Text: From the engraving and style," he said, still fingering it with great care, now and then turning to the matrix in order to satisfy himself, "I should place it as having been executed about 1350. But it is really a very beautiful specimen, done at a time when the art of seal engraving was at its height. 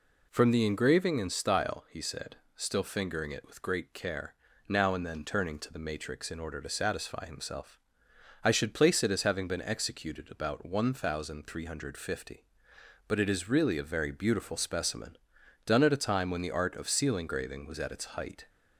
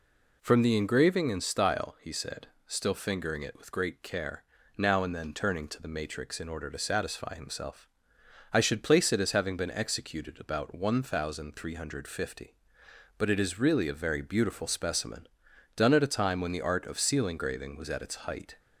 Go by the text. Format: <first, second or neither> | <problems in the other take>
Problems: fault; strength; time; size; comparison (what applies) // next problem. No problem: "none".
neither | none